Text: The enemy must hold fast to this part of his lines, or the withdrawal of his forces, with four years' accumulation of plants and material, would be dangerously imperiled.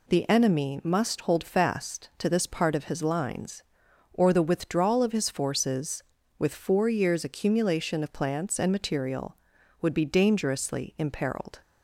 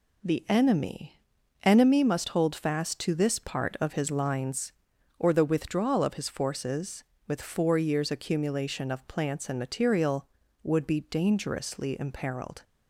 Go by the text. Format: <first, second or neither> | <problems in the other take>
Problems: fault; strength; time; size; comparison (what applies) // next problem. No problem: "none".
first | says "enemy" twice; at 1.6 s